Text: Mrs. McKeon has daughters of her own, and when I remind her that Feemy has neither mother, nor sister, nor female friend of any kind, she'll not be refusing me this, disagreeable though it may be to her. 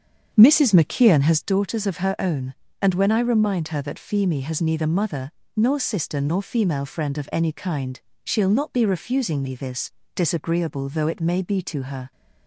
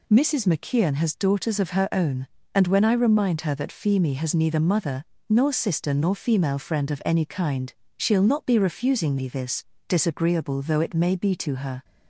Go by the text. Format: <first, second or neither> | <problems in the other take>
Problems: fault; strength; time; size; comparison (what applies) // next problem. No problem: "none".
second | starts louder than the rest; strong; until 1.6 s; 7.5 dB